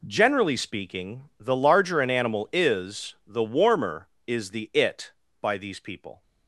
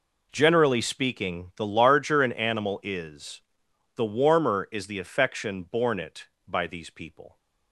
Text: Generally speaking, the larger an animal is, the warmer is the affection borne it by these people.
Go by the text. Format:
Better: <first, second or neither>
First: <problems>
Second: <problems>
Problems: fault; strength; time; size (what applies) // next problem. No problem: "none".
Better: second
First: skips "affection borne"; at 4.7 s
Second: none